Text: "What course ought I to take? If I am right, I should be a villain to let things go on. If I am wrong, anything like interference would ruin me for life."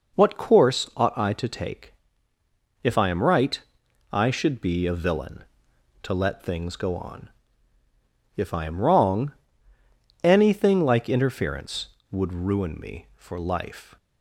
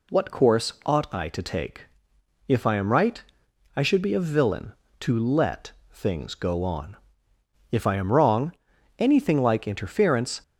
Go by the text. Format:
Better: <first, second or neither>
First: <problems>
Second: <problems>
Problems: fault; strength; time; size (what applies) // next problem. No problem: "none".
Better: first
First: none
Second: pauses between "let" and "things"; slight; at 5.7 s; 0.20 s long // stops before "would ruin me for life"; at 10.4 s